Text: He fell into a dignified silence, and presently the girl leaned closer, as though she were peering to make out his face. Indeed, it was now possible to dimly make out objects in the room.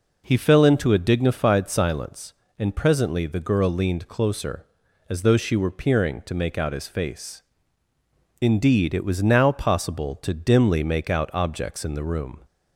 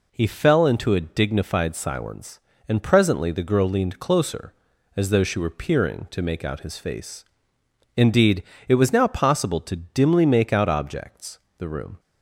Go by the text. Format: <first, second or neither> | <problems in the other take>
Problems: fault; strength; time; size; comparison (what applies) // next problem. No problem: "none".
first | skips "in"; at 11.4 s